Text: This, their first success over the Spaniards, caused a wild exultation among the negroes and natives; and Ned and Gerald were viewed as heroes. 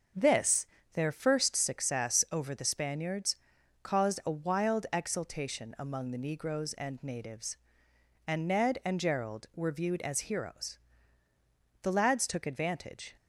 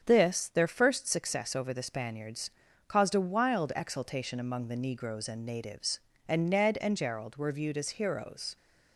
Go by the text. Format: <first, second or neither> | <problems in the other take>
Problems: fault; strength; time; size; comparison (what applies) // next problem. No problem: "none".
second | starts louder than the rest; until 1.4 s; 6.5 dB; strong in the second // goes on to say "The lads took advantage"; from 11.8 s on; 1.3 s long